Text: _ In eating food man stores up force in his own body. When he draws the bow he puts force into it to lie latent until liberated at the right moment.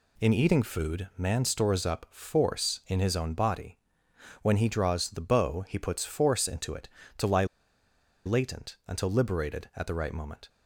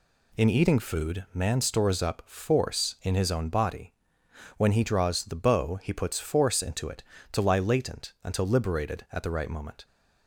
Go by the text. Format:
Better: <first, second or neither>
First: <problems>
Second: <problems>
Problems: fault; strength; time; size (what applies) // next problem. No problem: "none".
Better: second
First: pauses between "lie" and "latent"; noticeable; at 7.4 s; 0.81 s long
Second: none